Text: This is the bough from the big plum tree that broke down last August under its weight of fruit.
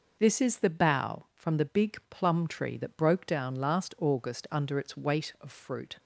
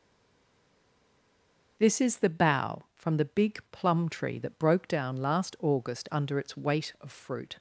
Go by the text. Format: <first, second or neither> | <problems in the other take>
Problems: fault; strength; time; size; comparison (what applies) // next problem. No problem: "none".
first | stays silent before the first word; noticeable; until 1.7 s; 1.7 s long